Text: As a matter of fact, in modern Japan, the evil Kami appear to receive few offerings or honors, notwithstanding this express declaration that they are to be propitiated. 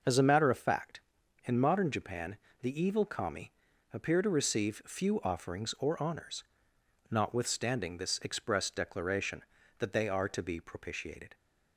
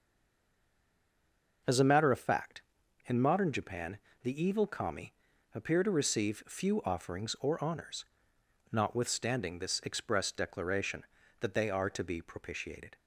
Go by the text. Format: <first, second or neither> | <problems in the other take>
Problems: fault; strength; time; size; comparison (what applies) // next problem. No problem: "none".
first | stays silent before the first word; noticeable; until 1.6 s; 1.6 s long // pauses between "Kami" and "appear"; at 5.1 s; 0.42 s long; also in the first